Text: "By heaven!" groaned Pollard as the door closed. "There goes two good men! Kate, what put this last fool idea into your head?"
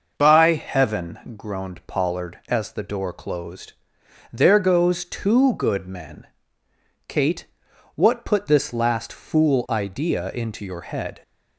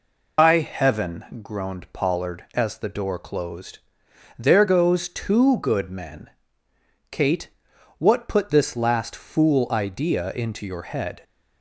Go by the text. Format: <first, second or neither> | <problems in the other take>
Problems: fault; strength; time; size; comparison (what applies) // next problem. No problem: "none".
first | loses the start of "By"; at 0.3 s; 145 ms